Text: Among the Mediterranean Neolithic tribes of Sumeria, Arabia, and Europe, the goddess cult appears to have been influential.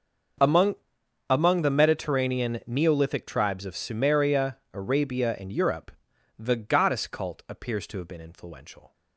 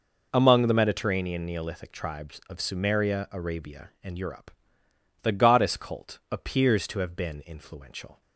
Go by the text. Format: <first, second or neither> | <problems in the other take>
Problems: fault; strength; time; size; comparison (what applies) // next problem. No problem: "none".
second | starts louder than the rest; until 1.9 s; 6.5 dB // says "Among" twice; at 1.2 s